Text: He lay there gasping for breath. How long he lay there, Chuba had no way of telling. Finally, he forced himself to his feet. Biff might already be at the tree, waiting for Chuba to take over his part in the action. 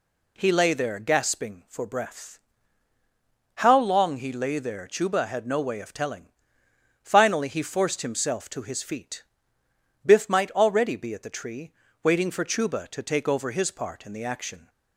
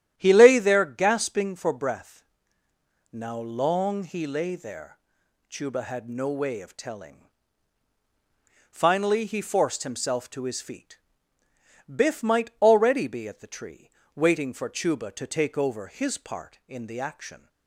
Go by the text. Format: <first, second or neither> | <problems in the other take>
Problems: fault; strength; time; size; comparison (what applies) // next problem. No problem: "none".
first | starts louder than the rest; strong; until 1.1 s; 10.5 dB // says "Now" for "How"; at 3.1 s